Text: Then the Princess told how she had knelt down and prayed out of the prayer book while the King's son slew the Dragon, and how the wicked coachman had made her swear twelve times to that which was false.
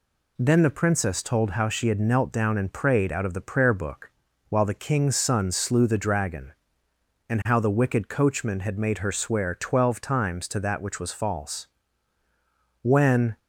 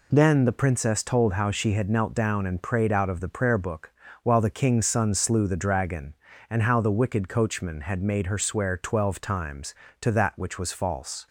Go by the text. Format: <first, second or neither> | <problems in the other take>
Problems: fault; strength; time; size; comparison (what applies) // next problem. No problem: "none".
second | pauses between "book" and "while"; at 4.1 s; 0.38 s long; slight in the second // goes on to say "When"; from 12.8 s on; 0.56 s long